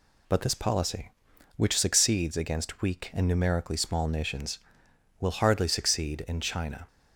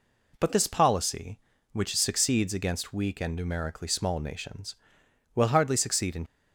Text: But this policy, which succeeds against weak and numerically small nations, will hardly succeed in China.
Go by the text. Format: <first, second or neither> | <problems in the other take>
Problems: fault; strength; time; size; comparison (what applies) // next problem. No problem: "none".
first | stops before "China"; at 6.2 s